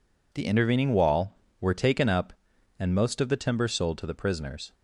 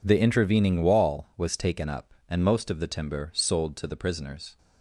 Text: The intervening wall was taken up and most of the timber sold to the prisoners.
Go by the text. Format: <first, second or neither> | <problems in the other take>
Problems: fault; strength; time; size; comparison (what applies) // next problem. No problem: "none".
second | says "were" for "was"; at 1.5 s